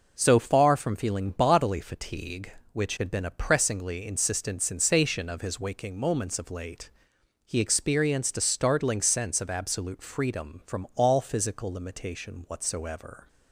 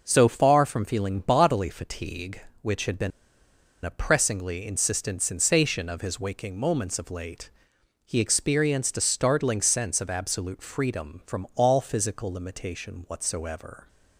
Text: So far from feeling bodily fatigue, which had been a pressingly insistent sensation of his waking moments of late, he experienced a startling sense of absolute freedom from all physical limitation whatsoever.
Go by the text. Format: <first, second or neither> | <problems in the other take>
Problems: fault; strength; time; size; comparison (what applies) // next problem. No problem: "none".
first | pauses between "been" and "a"; noticeable; at 3.1 s; 0.73 s long